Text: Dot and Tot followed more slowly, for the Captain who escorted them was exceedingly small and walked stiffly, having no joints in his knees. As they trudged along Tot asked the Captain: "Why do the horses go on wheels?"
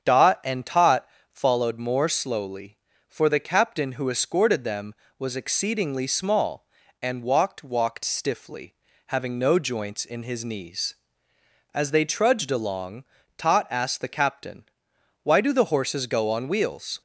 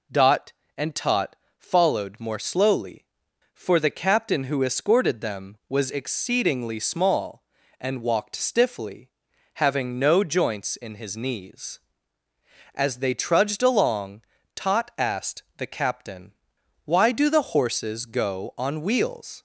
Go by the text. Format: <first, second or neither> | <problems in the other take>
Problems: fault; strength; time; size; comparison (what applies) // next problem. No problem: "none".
second | starts louder than the rest; strong; until 1.0 s; 8 dB // pauses between "Tot" and "followed"; slight; at 1.0 s; 0.24 s long; slight in the second // says "walked" twice; at 7.6 s // pauses between "along" and "Tot"; slight; at 13.0 s; 0.32 s long; slight in the second